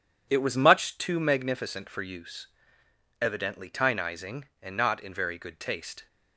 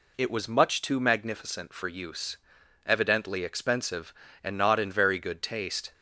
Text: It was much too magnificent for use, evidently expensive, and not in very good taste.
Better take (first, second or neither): second